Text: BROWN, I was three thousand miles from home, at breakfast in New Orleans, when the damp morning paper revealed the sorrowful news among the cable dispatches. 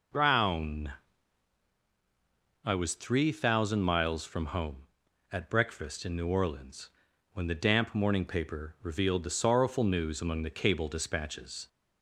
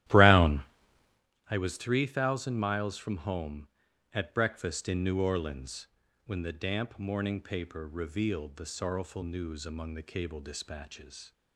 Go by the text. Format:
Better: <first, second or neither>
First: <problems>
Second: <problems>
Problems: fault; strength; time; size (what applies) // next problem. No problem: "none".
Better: first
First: none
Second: starts louder than the rest; strong; until 1.3 s; 13.5 dB